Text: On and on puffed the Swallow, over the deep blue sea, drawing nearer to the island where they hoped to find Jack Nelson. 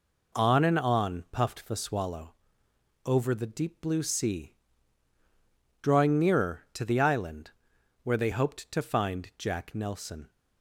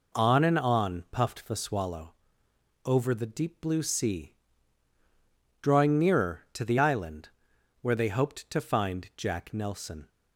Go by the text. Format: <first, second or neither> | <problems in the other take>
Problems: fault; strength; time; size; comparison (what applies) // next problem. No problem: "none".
neither | pauses between "island" and "where"; noticeable; the same in both